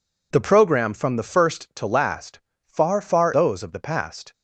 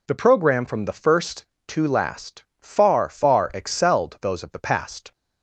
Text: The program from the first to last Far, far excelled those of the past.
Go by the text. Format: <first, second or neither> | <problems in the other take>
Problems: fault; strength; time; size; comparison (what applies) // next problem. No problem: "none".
second | pauses between "last" and "Far"; slight; at 2.4 s; 0.26 s long; slight in the second // skips "excelled"; at 3.3 s